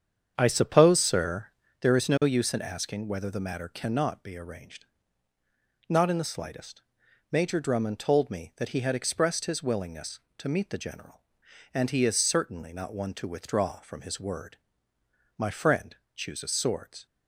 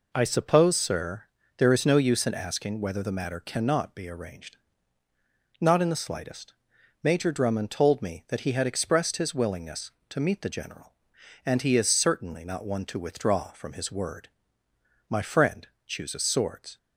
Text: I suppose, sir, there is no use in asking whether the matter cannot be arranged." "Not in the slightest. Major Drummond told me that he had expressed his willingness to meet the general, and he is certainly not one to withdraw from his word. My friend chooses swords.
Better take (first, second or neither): second